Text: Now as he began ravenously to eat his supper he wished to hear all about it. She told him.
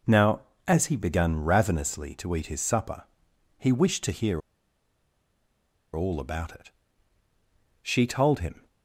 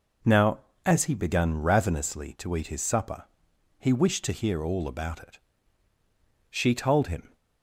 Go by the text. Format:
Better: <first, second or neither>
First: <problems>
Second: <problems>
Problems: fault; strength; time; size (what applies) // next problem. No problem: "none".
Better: second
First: pauses between "supper" and "he"; noticeable; at 3.0 s; 0.54 s long // pauses between "hear" and "all"; strong; at 4.4 s; 1.5 s long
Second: pauses between "supper" and "he"; noticeable; at 3.2 s; 0.54 s long